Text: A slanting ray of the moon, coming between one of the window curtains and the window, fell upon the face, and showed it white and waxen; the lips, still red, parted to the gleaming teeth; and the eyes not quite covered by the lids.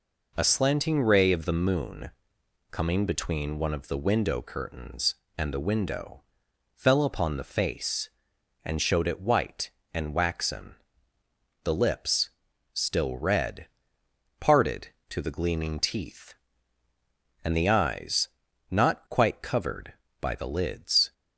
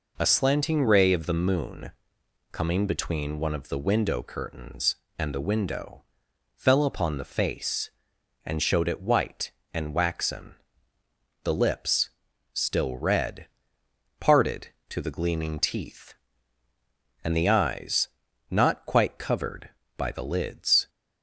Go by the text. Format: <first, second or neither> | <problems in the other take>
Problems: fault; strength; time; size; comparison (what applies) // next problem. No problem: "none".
neither | pauses between "eyes" and "not"; the same in both